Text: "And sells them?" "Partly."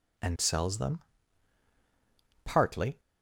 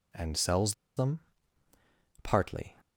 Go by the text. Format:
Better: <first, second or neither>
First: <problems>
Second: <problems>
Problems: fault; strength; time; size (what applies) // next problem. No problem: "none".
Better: first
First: none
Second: pauses between "sells" and "them"; slight; at 0.7 s; 0.23 s long